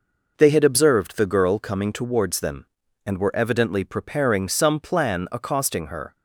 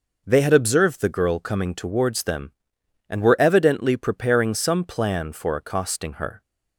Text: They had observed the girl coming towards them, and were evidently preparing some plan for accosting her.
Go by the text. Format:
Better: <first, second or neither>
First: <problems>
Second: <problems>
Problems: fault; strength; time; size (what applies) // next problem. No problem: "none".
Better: second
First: skips "for"; at 5.2 s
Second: none